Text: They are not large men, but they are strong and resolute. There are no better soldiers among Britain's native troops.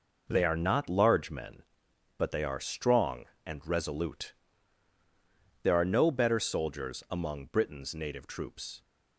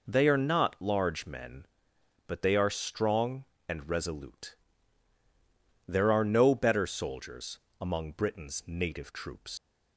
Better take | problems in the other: first | pauses between "soldiers" and "among"; slight; at 7.5 s; 0.22 s long // leaves "troops" unfinished; at 9.5 s; 115 ms

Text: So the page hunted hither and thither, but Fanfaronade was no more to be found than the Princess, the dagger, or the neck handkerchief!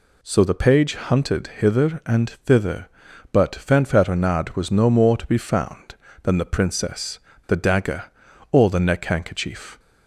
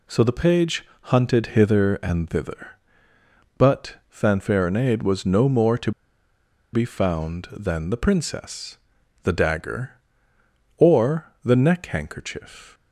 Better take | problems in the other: first | pauses between "page" and "hunted"; slight; at 0.8 s; 0.18 s long // pauses between "to" and "be"; noticeable; at 5.9 s; 0.81 s long

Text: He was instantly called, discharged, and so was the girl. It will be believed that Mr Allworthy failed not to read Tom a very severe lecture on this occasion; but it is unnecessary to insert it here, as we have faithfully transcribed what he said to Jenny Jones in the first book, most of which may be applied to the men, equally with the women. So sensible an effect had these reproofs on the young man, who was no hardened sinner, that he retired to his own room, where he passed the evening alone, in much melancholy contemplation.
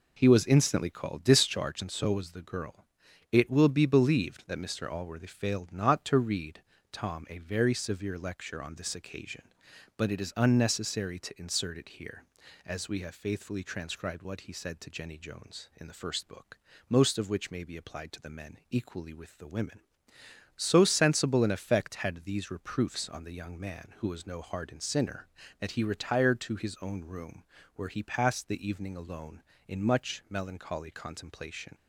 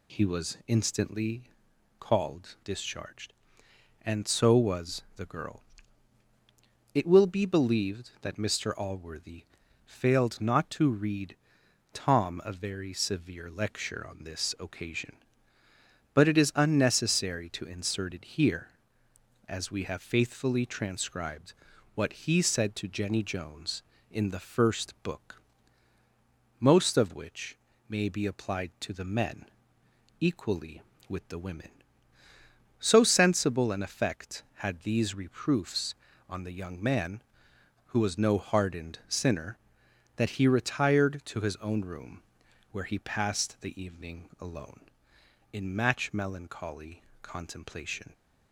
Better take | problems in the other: first | pauses between "instantly" and "called"; noticeable; at 1.4 s; 0.56 s long // pauses between "Allworthy" and "failed"; at 9.4 s; 0.40 s long // pauses between "read" and "Tom"; noticeable; at 11.3 s; 0.56 s long; slight in the first // pauses between "transcribed" and "what"; at 21.5 s; 0.42 s long // pauses between "which" and "may"; slight; at 27.5 s; 0.32 s long // says "match" for "much"; at 45.7 s // pauses between "melancholy" and "contemplation"; slight; at 47.0 s; 0.20 s long

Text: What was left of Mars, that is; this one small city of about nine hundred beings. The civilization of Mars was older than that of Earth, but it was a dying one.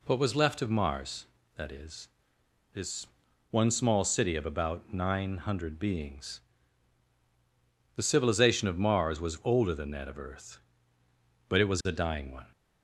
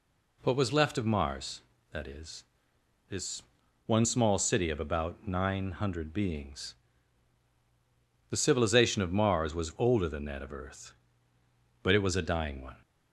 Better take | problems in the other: neither | pauses between "this" and "one"; noticeable; the same in both

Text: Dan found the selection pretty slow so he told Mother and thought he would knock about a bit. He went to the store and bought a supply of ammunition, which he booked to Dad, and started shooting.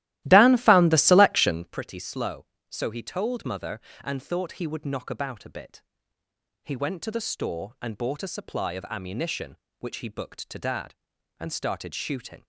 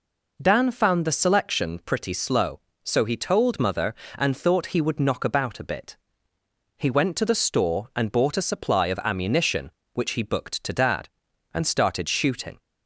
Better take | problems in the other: second | starts louder than the rest; strong; until 1.8 s; 15.5 dB

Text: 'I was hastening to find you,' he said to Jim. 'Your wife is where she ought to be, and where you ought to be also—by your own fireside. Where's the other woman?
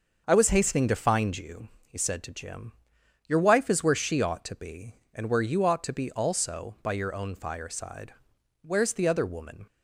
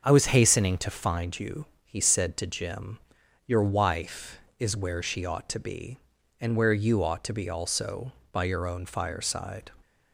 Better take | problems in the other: first | starts louder than the rest; until 1.0 s; 6.5 dB; also in the first // stops before "Where's the other woman"; at 9.8 s

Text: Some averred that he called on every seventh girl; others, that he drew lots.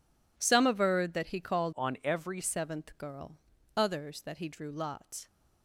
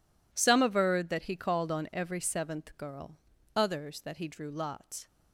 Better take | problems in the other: second | changes voice from "on" to "every"; from 1.7 to 2.3 s; 0.6 s long

